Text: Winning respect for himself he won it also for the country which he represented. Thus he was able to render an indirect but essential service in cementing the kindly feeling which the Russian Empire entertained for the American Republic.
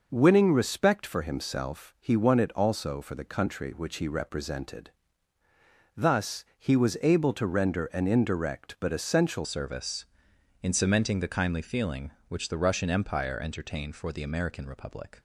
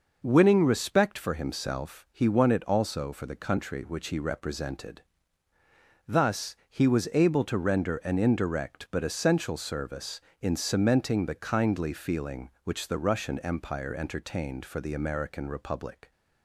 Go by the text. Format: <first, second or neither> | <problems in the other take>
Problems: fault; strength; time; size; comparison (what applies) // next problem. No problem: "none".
second | changes voice at "service"; from 9.4 s on; 5.7 s long